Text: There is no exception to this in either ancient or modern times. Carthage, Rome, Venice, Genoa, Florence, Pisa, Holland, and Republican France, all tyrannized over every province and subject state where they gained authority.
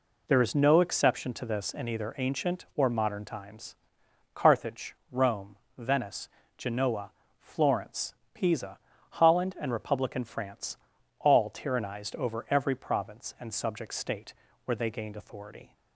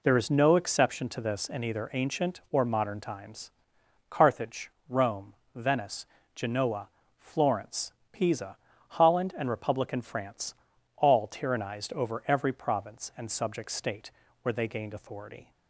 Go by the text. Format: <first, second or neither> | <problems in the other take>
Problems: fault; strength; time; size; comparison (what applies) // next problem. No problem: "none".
neither | pauses between "state" and "where"; slight; the same in both